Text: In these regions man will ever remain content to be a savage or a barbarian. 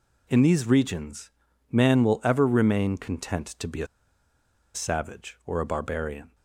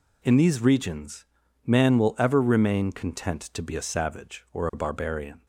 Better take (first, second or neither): second